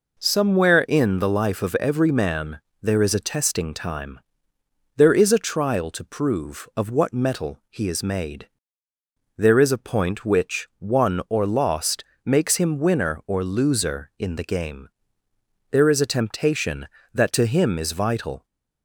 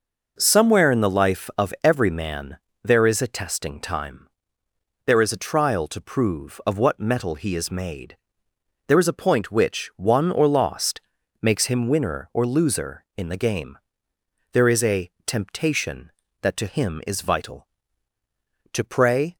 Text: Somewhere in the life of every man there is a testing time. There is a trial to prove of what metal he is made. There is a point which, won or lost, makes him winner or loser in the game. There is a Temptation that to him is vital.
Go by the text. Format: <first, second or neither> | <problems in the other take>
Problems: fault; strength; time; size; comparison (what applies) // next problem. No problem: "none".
first | pauses between "man" and "there"; slight; at 2.5 s; 0.24 s long; slight in the first // pauses between "a" and "Temptation"; slight; at 15.0 s; 0.16 s long // goes on to say "To pray"; noticeable; from 18.7 s on; 0.64 s long